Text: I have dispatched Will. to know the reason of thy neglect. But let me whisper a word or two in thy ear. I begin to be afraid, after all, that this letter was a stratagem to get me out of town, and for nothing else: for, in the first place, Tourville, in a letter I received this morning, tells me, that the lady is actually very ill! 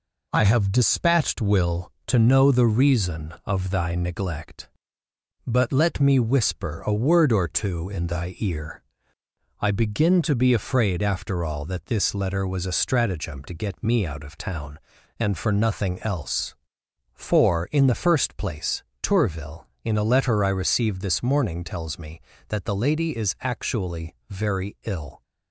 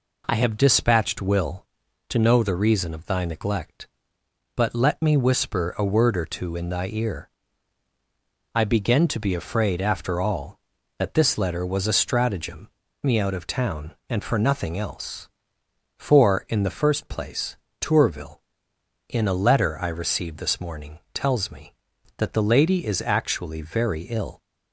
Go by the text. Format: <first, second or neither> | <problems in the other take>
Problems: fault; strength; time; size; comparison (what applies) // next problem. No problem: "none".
first | skips "to get"; at 12.8 s